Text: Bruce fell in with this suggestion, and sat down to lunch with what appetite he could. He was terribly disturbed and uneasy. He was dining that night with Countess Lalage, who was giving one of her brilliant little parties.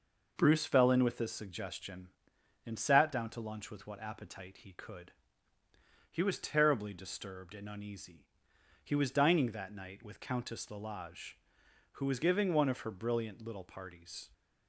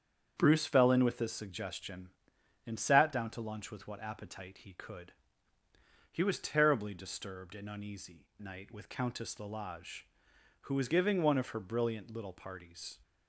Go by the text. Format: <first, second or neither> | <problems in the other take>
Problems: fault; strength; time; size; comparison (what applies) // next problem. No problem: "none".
first | starts louder than the rest; strong; until 1.3 s; 7.5 dB // skips "He was dining that"; at 8.3 s